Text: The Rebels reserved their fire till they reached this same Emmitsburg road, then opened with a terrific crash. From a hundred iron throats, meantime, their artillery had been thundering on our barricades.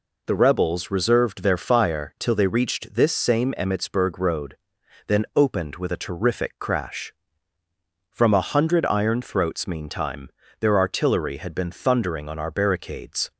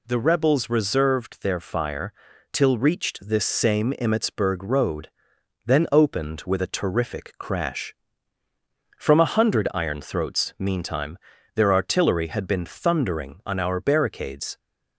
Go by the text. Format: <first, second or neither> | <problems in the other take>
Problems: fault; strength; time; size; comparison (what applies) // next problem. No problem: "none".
first | pauses between "fire" and "till"; at 2.1 s; 0.40 s long // skips "they"; at 2.7 s